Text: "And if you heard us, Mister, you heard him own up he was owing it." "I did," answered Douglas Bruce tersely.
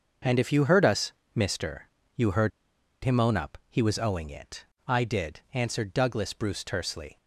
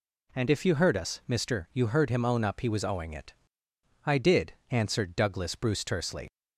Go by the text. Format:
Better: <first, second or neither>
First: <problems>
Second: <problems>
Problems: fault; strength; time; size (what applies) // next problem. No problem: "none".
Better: second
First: starts louder than the rest; until 1.5 s; 6 dB // pauses between "heard" and "him"; noticeable; at 2.5 s; 0.54 s long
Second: none